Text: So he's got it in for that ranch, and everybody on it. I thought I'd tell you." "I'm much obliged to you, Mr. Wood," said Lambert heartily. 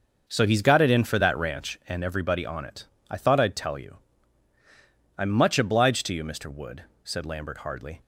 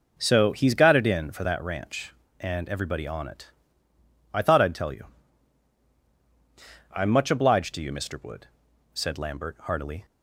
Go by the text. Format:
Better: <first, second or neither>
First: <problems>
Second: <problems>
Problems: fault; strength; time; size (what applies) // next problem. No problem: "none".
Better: second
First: starts louder than the rest; until 1.3 s; 6 dB // says "hardly" for "heartily"; at 7.5 s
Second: none